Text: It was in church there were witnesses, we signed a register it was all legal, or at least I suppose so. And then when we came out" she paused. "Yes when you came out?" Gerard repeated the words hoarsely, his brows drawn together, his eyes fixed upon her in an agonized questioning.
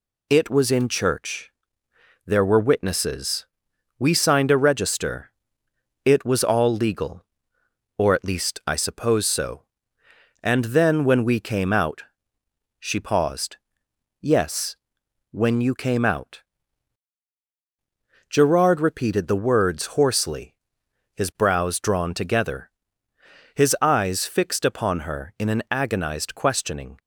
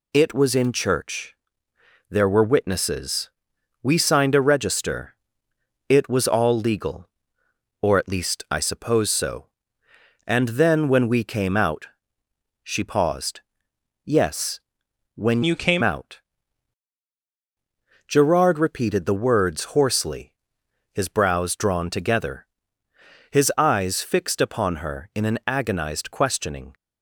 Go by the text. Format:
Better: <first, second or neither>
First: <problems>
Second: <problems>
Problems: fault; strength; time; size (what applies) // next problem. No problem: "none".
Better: first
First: pauses between "church" and "there"; noticeable; at 1.5 s; 0.76 s long // pauses between "register" and "it"; noticeable; at 5.3 s; 0.76 s long // pauses between "out" and "she"; noticeable; at 12.0 s; 0.74 s long // pauses between "Yes" and "when"; noticeable; at 14.7 s; 0.54 s long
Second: pauses between "church" and "there"; noticeable; at 1.3 s; 0.76 s long // pauses between "register" and "it"; noticeable; at 5.1 s; 0.76 s long // pauses between "out" and "she"; noticeable; at 11.8 s; 0.74 s long // pauses between "Yes" and "when"; noticeable; at 14.5 s; 0.54 s long // changes voice from "you" to "came"; from 15.4 to 15.8 s; 0.4 s long